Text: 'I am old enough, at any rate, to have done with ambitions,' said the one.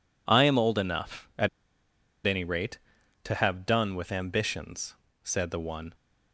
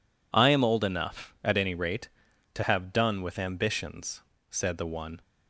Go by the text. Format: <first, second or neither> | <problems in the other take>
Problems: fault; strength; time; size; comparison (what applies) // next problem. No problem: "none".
second | pauses between "at" and "any"; noticeable; at 1.4 s; 0.78 s long